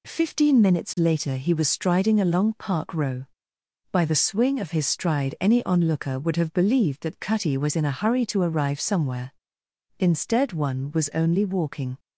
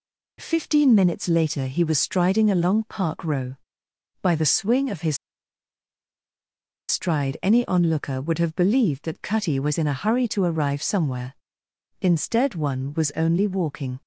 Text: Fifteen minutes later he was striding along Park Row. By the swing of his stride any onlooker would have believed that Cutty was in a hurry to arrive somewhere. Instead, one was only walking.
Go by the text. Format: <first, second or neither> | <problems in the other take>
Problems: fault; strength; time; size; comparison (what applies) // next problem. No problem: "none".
first | pauses between "his" and "stride"; strong; at 5.1 s; 1.7 s long